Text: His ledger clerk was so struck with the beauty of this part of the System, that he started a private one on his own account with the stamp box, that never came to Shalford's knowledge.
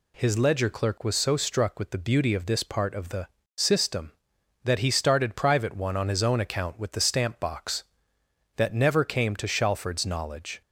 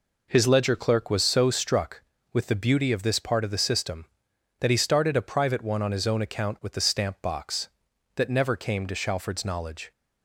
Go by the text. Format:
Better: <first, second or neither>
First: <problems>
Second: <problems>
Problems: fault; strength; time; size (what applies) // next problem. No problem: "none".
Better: second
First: pauses between "the" and "System"; slight; at 3.2 s; 0.32 s long // skips "a"; at 5.3 s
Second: none